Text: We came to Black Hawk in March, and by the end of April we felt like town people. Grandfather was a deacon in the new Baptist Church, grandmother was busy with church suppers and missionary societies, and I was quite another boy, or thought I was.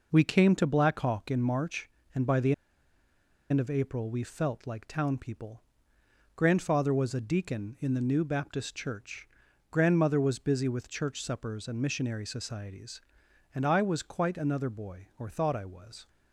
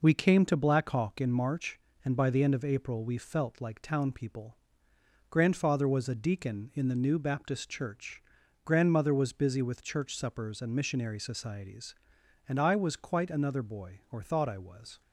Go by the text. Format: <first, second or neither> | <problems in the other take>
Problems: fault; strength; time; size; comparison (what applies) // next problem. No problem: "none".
second | pauses between "the" and "end"; at 2.5 s; 0.98 s long